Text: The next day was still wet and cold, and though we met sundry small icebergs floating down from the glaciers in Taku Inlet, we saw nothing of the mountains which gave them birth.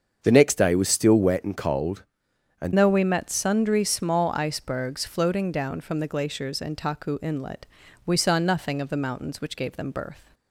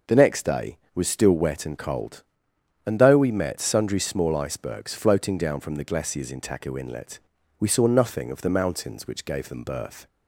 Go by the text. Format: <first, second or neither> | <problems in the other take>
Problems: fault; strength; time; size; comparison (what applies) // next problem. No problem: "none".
second | starts louder than the rest; until 1.2 s; 7 dB // changes voice at "though"; from 2.7 s on; 7.6 s long